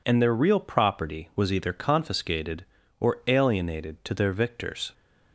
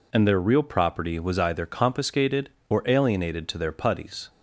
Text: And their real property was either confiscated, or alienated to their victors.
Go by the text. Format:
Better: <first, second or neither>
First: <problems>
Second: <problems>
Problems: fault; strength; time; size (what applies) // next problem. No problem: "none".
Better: first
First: none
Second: says "putties" for "victors"; at 3.7 s